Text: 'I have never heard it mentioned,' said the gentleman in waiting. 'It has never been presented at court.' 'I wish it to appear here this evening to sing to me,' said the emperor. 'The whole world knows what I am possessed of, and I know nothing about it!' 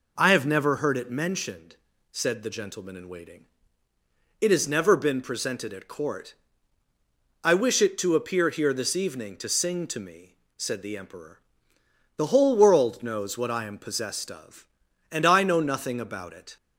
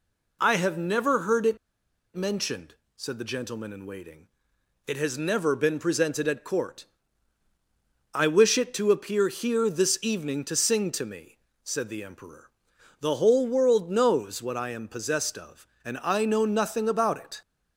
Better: first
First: none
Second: pauses between "it" and "mentioned"; noticeable; at 1.5 s; 0.57 s long

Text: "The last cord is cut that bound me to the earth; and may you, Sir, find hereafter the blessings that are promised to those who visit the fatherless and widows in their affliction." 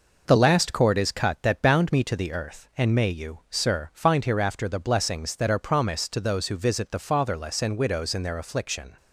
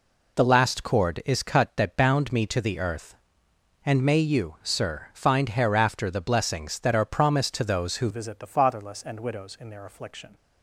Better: first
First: none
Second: changes voice at "visit"; from 8.1 s on; 2.2 s long

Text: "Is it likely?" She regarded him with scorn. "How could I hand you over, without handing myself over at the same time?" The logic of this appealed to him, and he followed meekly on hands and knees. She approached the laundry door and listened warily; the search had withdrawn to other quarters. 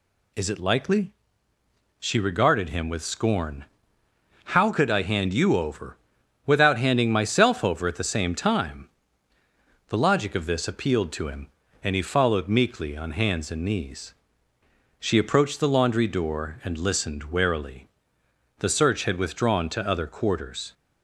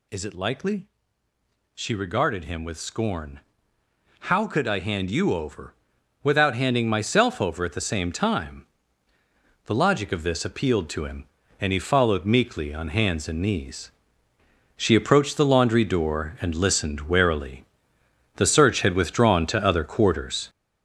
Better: first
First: none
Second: gets louder; throughout; 6.5 dB

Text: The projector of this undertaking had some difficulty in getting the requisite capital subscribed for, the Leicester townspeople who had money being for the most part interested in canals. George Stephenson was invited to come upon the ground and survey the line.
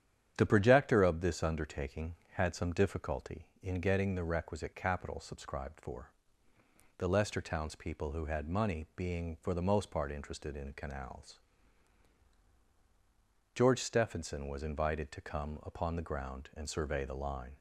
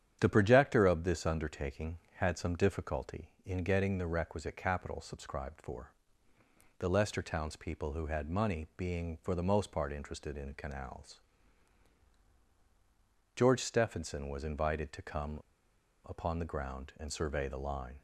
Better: first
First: starts louder than the rest; strong; until 1.3 s; 9 dB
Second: starts louder than the rest; strong; until 1.2 s; 9 dB // pauses between "come" and "upon"; noticeable; at 15.3 s; 0.70 s long

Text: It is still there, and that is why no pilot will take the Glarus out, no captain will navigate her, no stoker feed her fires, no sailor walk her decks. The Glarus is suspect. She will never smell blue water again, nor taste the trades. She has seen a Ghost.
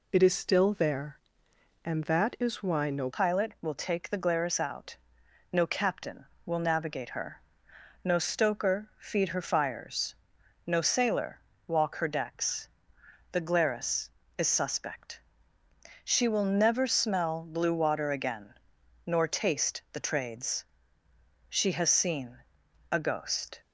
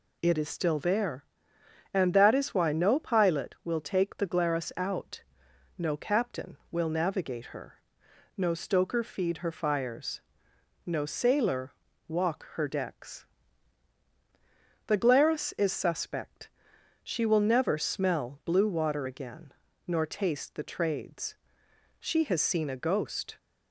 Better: second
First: changes voice at "pilot"; from 3.1 s on; 20.5 s long // pauses between "sailor" and "walk"; slight; at 11.4 s; 0.26 s long // pauses between "seen" and "a"; noticeable; at 22.4 s; 0.52 s long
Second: pauses between "sailor" and "walk"; slight; at 11.7 s; 0.36 s long

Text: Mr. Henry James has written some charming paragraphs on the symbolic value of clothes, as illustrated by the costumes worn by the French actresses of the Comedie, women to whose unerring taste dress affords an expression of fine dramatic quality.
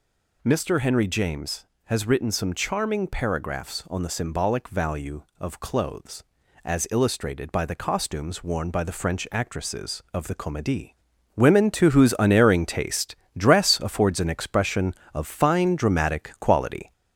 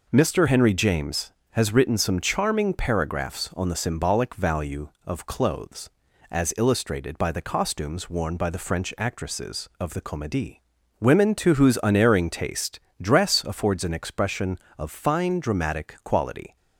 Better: second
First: gets louder; slight; throughout; 3 dB // pauses between "taste" and "dress"; slight; at 13.1 s; 0.24 s long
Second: pauses between "taste" and "dress"; slight; at 12.7 s; 0.24 s long

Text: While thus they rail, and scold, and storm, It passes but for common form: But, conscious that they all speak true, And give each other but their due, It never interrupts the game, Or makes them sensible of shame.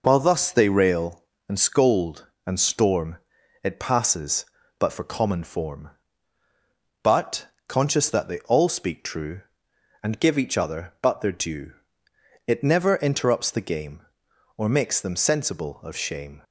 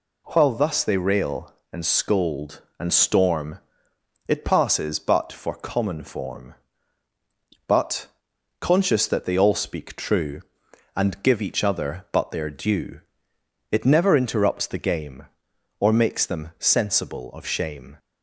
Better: neither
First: none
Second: none

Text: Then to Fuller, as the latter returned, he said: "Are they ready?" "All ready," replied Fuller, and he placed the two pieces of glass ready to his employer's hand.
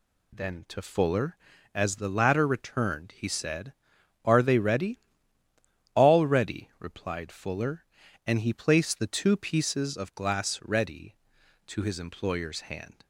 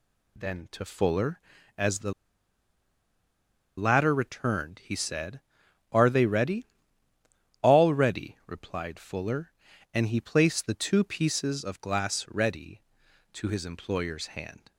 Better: first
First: none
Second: pauses between "the" and "latter"; strong; at 2.1 s; 1.6 s long

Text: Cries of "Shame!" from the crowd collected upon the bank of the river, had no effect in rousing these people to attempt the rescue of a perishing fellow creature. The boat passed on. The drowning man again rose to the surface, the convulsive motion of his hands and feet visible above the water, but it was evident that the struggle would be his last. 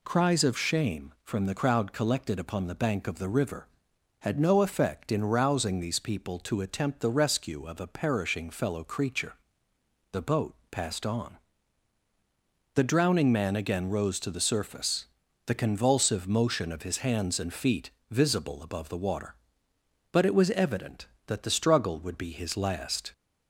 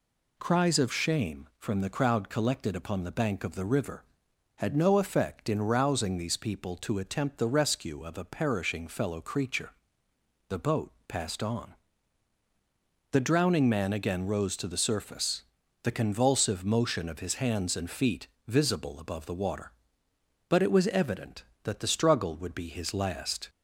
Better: neither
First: pauses between "boat" and "passed"; slight; at 10.5 s; 0.16 s long // pauses between "feet" and "visible"; slight; at 17.8 s; 0.20 s long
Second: pauses between "boat" and "passed"; slight; at 10.9 s; 0.16 s long // pauses between "feet" and "visible"; slight; at 18.2 s; 0.20 s long

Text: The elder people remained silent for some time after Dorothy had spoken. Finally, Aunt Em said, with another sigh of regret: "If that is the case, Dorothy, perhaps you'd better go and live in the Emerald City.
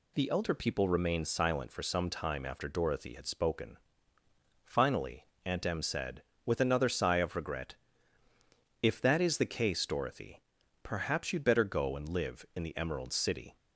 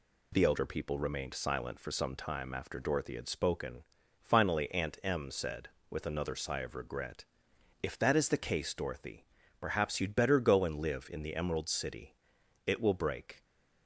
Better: first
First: none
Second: goes on to say "It will break"; noticeable; from 12.6 s on; 0.78 s long

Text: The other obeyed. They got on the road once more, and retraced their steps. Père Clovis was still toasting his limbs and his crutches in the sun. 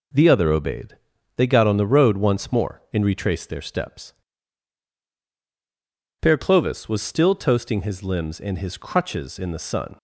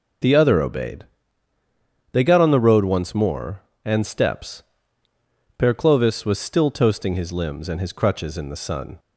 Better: first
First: none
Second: skips "retraced their"; at 4.0 s

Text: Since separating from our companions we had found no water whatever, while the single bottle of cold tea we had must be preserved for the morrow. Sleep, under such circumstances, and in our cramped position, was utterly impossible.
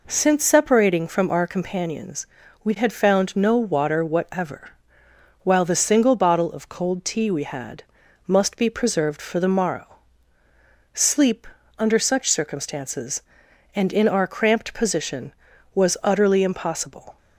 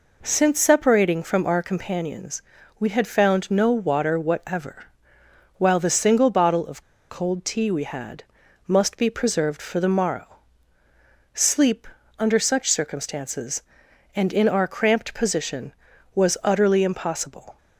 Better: first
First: pauses between "companions" and "we"; slight; at 2.2 s; 0.36 s long // pauses between "had" and "must"; at 7.8 s; 0.42 s long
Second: pauses between "companions" and "we"; slight; at 2.4 s; 0.36 s long // pauses between "of" and "cold"; slight; at 6.8 s; 0.25 s long // pauses between "had" and "must"; at 8.2 s; 0.42 s long

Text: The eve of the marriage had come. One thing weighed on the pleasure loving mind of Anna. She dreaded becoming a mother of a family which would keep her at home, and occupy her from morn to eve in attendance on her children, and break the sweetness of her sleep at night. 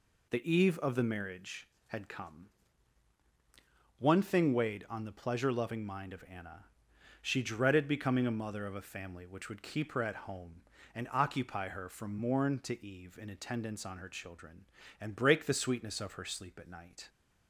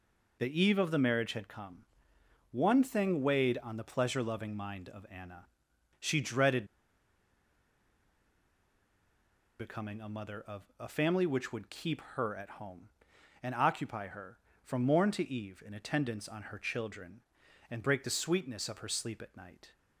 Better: first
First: none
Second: pauses between "dreaded" and "becoming"; strong; at 6.6 s; 2.9 s long // pauses between "of" and "a"; slight; at 10.6 s; 0.16 s long

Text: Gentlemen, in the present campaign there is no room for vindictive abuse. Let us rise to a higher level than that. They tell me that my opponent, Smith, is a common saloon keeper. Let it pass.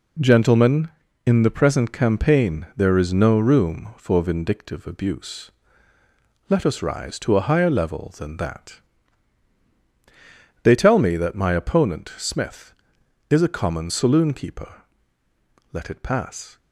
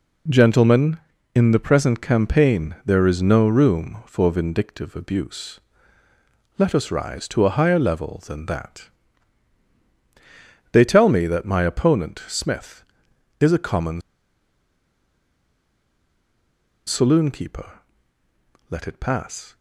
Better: first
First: none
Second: pauses between "common" and "saloon"; strong; at 14.0 s; 2.8 s long

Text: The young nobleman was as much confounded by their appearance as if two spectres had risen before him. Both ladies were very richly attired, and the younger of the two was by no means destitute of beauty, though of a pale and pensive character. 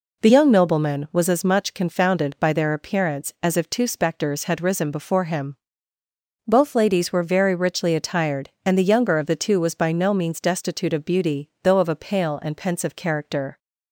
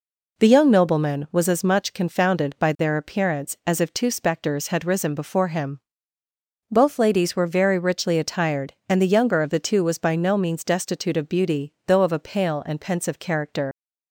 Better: first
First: none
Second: leaves "character" unfinished; at 13.7 s; 110 ms

